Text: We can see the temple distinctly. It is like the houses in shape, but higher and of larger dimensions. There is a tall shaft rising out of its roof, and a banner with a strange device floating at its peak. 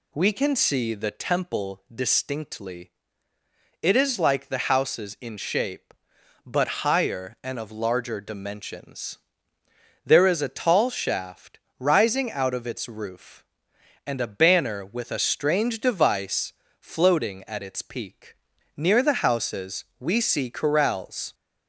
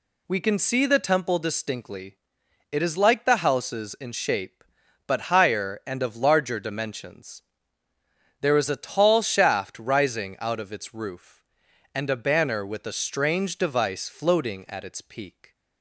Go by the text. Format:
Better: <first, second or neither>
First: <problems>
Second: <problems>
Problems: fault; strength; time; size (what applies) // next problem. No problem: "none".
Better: second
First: pauses between "shaft" and "rising"; slight; at 11.5 s; 0.18 s long // pauses between "device" and "floating"; slight; at 16.5 s; 0.26 s long // goes on to say "Near the houses we see corrals"; strong; from 18.7 s on; 2.5 s long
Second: none